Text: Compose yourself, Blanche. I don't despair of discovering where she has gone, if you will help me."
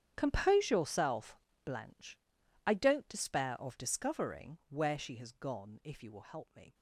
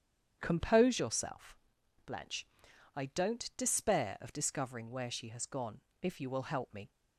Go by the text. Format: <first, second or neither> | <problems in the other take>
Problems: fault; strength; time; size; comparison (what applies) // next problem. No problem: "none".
second | gets quieter; strong; throughout; 16 dB // starts louder than the rest; strong; until 1.1 s; 9 dB; strong in the second